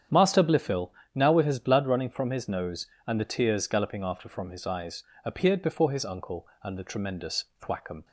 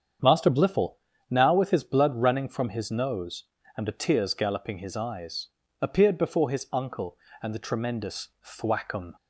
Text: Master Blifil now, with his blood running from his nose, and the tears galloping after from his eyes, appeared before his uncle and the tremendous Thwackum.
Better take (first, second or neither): first